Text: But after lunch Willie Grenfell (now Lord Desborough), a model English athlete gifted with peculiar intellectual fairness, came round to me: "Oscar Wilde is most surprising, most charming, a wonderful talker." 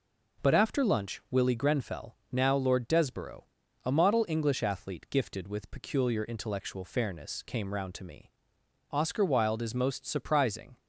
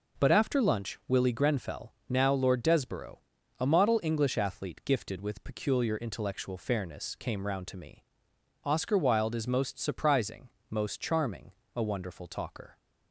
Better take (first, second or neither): second